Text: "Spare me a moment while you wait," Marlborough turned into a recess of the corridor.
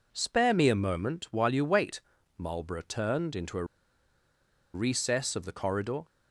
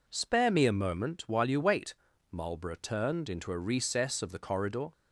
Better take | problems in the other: second | pauses between "a" and "recess"; at 3.6 s; 1.0 s long

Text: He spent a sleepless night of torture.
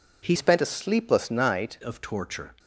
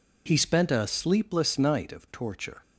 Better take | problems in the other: second | changes voice from "spent" to "night"; from 0.3 to 1.7 s; 1.4 s long

